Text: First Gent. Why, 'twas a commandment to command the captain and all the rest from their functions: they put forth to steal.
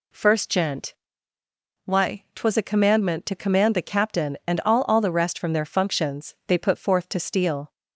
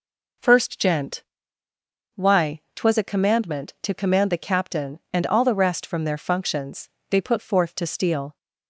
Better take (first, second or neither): second